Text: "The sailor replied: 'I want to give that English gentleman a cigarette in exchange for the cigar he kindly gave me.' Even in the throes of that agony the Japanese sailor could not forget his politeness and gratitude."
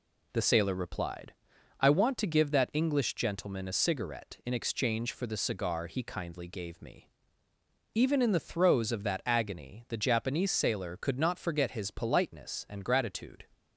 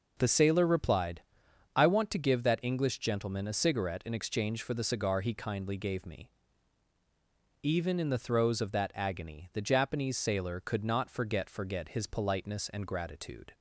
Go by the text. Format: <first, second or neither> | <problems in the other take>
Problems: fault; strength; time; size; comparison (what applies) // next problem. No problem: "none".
first | says "forget" twice; at 11.4 s